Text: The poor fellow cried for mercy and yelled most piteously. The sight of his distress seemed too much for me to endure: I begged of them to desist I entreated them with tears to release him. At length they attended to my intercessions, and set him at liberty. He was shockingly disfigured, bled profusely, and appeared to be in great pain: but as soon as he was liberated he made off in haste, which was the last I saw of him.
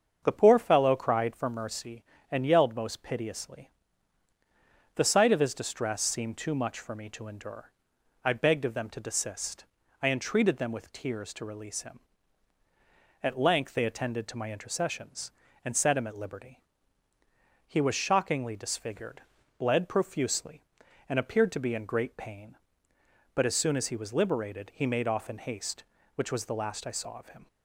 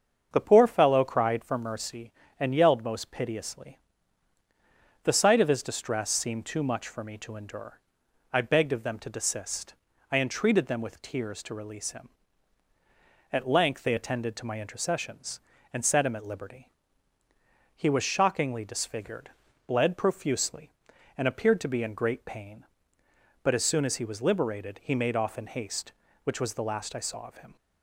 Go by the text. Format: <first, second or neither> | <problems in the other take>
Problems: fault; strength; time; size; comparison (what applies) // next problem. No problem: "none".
neither | starts louder than the rest; the same in both // pauses between "desist" and "I"; the same in both